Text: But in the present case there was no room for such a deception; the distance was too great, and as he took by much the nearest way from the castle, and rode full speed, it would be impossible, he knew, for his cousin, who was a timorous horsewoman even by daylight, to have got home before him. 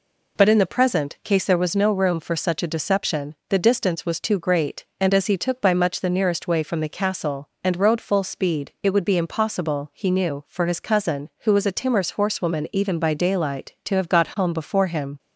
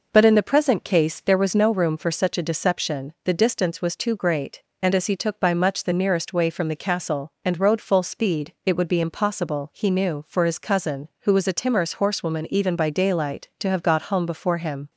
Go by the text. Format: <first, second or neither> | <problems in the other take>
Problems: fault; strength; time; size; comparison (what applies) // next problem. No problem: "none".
neither | none